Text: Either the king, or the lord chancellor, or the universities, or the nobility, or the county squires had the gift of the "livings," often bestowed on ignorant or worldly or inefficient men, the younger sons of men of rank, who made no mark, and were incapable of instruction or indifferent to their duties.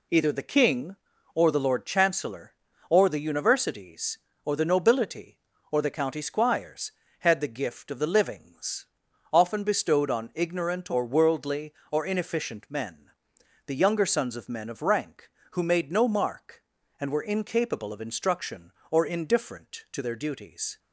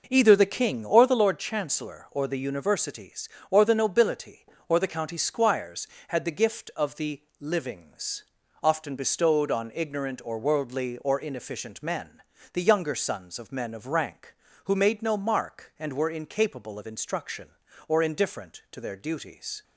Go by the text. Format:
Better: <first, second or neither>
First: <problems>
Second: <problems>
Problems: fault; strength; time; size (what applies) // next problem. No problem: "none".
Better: first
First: none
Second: starts louder than the rest; noticeable; until 1.2 s; 5.5 dB // pauses between "the" and "livings"; slight; at 7.2 s; 0.16 s long